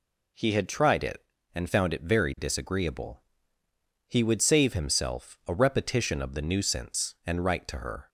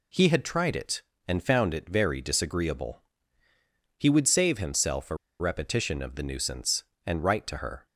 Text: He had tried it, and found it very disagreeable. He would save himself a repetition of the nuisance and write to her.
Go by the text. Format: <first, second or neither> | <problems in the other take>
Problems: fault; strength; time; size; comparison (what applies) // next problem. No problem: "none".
first | pauses between "a" and "repetition"; slight; at 5.1 s; 0.24 s long